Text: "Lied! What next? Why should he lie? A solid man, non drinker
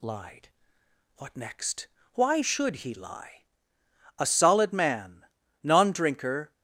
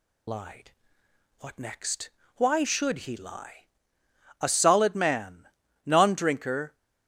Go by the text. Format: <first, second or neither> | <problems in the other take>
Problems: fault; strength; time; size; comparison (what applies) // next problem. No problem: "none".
first | loses the start of "Lied"; at 0.2 s; 25 ms